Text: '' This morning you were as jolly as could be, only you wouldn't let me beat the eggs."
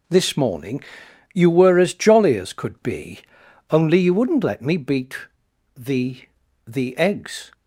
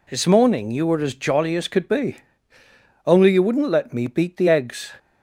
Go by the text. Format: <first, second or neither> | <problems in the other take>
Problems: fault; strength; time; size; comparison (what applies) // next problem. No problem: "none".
second | pauses between "morning" and "you"; noticeable; at 0.8 s; 0.50 s long // pauses between "beat" and "the"; noticeable; at 5.1 s; 0.58 s long // says "the" twice; at 6.6 s